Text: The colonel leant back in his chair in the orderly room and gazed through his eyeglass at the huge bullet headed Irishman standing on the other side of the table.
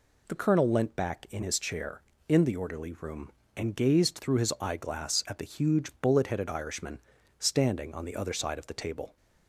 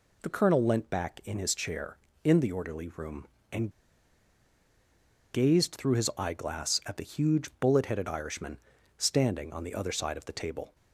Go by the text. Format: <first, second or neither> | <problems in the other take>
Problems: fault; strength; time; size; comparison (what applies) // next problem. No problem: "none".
first | pauses between "and" and "gazed"; strong; at 3.7 s; 1.6 s long // pauses between "Irishman" and "standing"; at 8.5 s; 0.38 s long; also in the first